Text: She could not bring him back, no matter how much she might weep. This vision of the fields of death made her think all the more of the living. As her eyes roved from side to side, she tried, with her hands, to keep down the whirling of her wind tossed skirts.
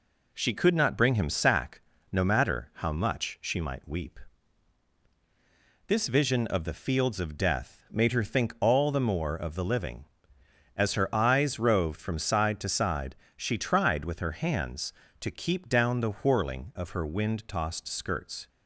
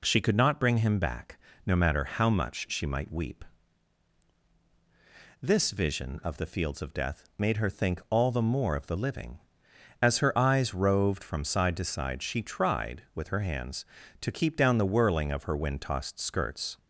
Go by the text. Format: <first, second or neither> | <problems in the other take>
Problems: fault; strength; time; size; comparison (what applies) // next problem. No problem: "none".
second | says "sack" for "back"; at 1.2 s